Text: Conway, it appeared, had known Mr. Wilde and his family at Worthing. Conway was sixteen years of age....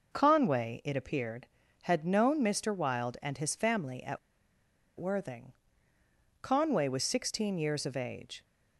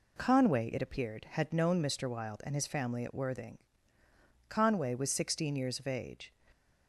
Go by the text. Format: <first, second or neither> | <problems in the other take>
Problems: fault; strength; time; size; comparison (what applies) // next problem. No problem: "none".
second | pauses between "at" and "Worthing"; noticeable; at 4.1 s; 0.80 s long